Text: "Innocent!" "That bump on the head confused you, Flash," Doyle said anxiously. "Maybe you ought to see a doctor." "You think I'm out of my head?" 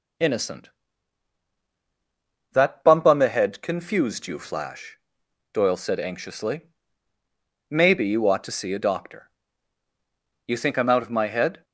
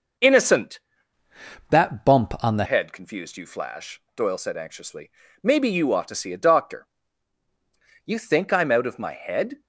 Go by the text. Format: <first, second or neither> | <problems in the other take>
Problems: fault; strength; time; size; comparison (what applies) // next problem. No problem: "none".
first | changes voice from "That" to "the"; from 1.6 to 2.6 s; 1.0 s long